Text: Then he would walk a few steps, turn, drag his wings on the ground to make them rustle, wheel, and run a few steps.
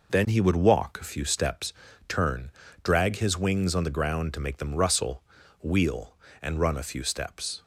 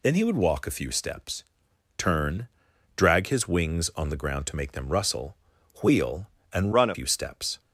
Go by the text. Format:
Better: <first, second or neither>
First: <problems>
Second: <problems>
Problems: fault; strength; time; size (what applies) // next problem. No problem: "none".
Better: first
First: none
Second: changes voice from "run" to "a"; from 6.7 to 6.9 s; 0.2 s long